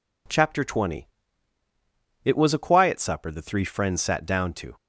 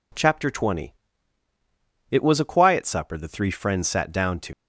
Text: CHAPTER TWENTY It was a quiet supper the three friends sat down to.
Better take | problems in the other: first | pauses between "TWENTY" and "It"; at 0.9 s; 1.1 s long; also in the first // leaves "to" unfinished; at 4.5 s; 90 ms

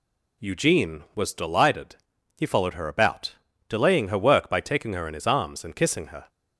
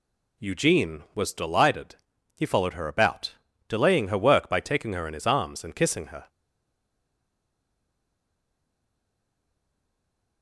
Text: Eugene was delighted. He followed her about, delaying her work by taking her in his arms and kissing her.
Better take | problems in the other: first | stays silent after the last word; strong; from 6.2 s on; 4.2 s long

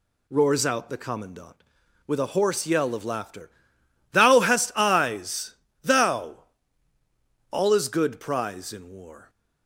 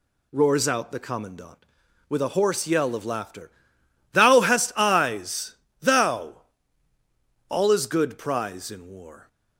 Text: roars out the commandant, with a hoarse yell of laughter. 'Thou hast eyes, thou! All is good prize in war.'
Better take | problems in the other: neither | none

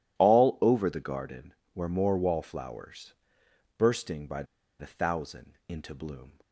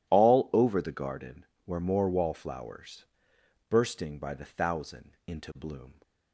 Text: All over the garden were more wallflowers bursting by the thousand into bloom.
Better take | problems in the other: second | pauses between "wallflowers" and "bursting"; noticeable; at 3.1 s; 0.64 s long; noticeable in the second // pauses between "by" and "the"; slight; at 4.4 s; 0.35 s long

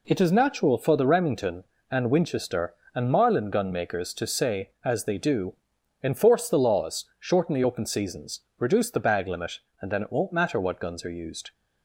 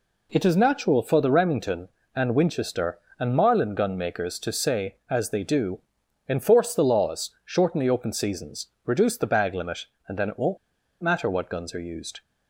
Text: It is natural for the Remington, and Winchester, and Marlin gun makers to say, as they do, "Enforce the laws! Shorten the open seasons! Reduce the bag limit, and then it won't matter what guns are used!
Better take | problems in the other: first | pauses between "won't" and "matter"; at 10.5 s; 0.45 s long

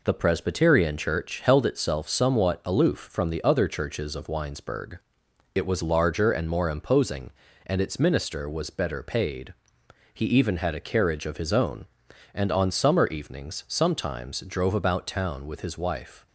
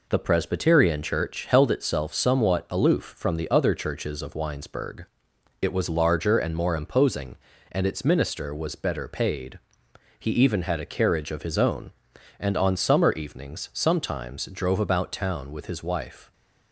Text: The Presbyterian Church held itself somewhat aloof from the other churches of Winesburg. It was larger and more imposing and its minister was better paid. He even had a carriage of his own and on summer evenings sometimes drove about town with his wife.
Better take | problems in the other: neither | none

